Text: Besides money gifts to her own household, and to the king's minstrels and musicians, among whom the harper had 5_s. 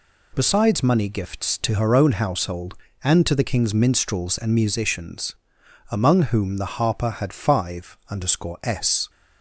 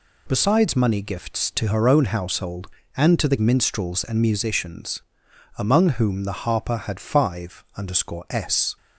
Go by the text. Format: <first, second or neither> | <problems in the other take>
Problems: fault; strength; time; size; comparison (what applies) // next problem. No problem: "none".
first | skips "king's"; at 3.3 s